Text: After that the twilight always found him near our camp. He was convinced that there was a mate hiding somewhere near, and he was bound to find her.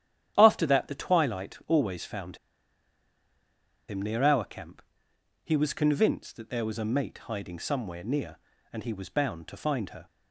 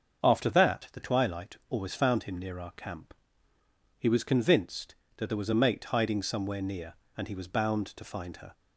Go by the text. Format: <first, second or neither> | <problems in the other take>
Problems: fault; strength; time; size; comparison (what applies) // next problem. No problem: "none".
second | starts louder than the rest; strong; until 1.3 s; 10.5 dB; also in the second // pauses between "found" and "him"; strong; at 2.3 s; 1.5 s long